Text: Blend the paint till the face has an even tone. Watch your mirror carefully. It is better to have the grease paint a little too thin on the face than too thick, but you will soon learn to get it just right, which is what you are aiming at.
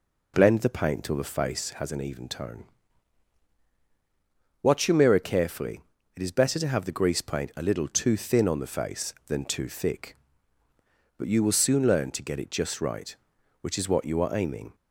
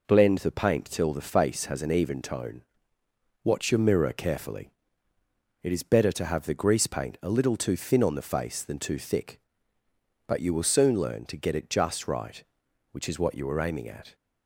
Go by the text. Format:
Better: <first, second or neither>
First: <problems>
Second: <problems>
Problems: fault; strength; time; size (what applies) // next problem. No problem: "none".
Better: second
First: stops before "at"; at 14.7 s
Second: none